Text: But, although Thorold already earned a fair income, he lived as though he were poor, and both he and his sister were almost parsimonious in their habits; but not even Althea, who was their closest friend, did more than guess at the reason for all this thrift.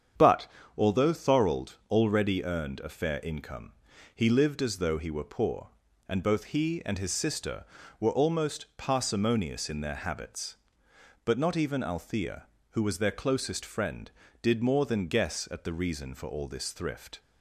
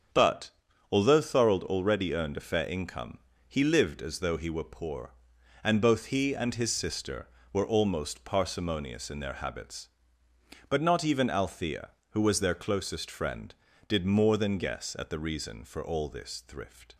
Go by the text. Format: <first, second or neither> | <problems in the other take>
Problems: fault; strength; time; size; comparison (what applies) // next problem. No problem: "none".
neither | starts louder than the rest; strong; the same in both